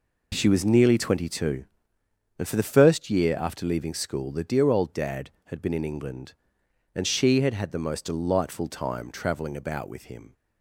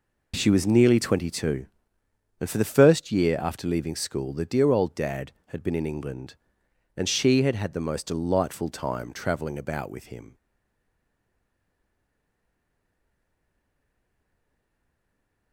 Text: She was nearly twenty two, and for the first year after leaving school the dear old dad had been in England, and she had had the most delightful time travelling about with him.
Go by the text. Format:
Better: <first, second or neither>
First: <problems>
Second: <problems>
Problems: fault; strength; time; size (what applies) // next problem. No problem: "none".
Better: first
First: none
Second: stays silent after the last word; strong; from 10.3 s on; 5.2 s long